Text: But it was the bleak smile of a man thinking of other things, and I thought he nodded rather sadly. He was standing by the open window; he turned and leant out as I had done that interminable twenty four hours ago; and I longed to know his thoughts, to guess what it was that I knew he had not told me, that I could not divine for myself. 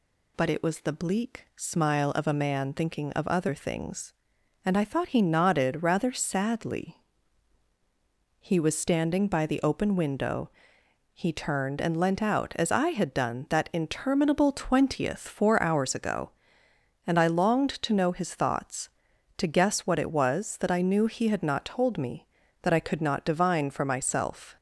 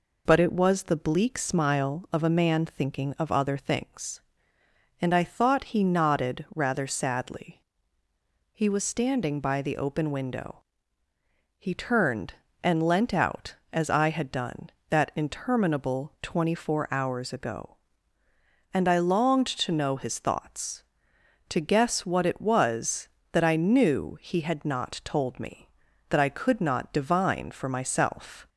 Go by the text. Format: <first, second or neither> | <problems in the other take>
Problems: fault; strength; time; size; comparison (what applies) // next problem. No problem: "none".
second | says "twentieth" for "twenty"; at 14.5 s